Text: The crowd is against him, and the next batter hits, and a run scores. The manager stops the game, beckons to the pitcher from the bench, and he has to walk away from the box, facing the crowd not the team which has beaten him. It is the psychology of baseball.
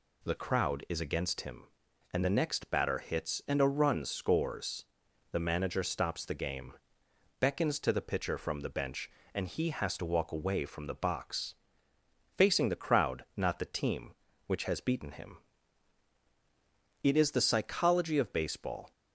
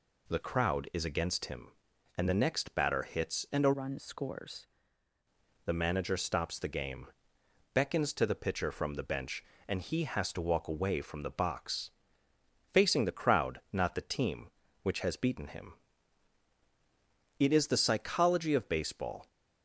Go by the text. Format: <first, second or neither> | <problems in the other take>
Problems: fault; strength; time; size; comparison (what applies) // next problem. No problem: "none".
first | changes voice from "run" to "scores"; from 3.7 to 4.6 s; 0.9 s long